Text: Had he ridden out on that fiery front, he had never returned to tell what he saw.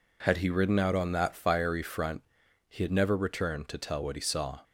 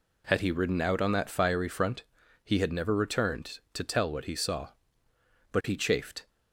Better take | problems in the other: first | goes on to say "But he chafed"; noticeable; from 5.5 s on; 0.76 s long

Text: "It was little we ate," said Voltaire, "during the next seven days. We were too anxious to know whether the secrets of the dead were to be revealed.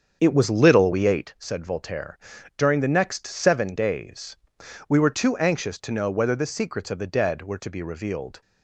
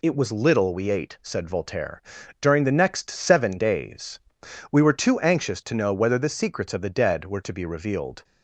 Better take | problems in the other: second | starts louder than the rest; strong; until 1.3 s; 7.5 dB

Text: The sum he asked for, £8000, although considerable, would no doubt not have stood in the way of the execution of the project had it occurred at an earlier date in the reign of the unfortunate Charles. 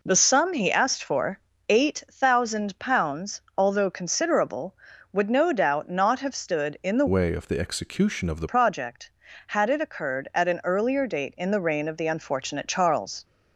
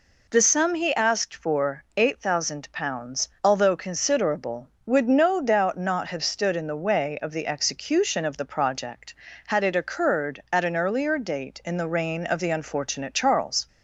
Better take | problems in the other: second | changes voice from "way" to "the"; from 7.0 to 8.4 s; 1.4 s long

